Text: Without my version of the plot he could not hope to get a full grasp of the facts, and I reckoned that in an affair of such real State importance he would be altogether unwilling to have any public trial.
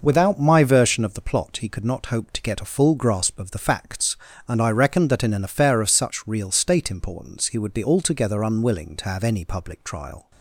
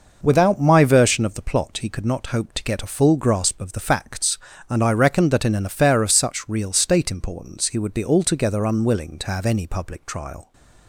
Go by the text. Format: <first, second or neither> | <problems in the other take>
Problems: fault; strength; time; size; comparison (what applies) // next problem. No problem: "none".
neither | none